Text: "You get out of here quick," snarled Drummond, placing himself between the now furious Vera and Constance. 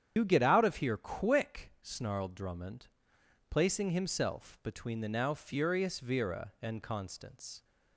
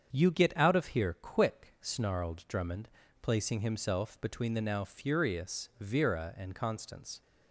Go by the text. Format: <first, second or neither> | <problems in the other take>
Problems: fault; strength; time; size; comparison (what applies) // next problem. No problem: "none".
second | loses the start of "You"; at 0.1 s; 80 ms // starts louder than the rest; strong; until 1.1 s; 9 dB; strong in the second